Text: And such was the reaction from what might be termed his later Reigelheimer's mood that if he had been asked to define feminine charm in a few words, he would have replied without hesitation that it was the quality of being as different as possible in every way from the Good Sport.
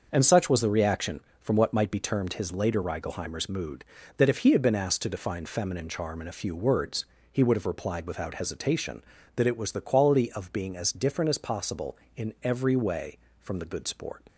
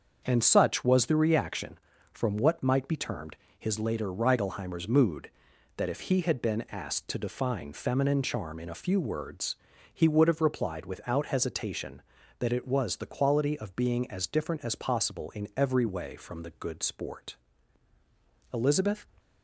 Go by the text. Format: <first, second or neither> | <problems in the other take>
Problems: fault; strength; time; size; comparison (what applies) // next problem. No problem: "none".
first | starts louder than the rest; until 1.2 s; 7 dB; also in the first // pauses between "termed" and "his"; slight; at 3.3 s; 0.22 s long // goes on to say "Elizabeth"; from 18.5 s on; 0.52 s long